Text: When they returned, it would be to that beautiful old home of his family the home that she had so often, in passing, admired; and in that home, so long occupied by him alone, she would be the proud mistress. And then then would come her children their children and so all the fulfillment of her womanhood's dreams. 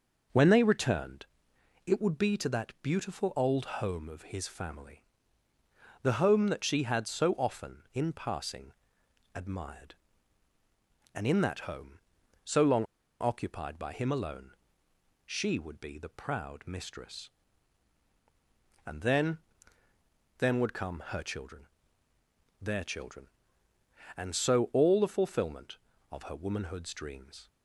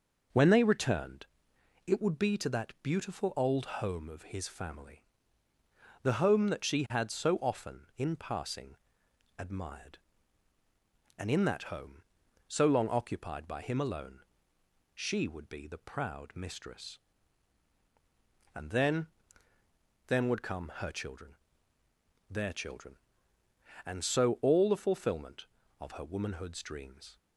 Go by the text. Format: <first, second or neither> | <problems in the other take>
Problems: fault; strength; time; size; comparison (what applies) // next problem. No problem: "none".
second | starts louder than the rest; noticeable; until 1.9 s; 6 dB; noticeable in the second // pauses between "family" and "the"; at 5.0 s; 1.0 s long; also in the second // pauses between "long" and "occupied"; slight; at 12.8 s; 0.34 s long // pauses between "then" and "then"; at 19.3 s; 1.0 s long; also in the second // pauses between "children" and "their"; noticeable; at 21.6 s; 0.94 s long; noticeable in the second